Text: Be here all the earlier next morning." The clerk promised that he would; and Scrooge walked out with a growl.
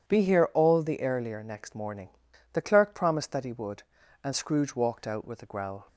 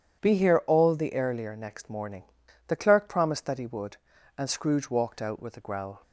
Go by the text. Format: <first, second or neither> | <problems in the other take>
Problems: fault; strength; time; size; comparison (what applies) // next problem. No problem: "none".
neither | none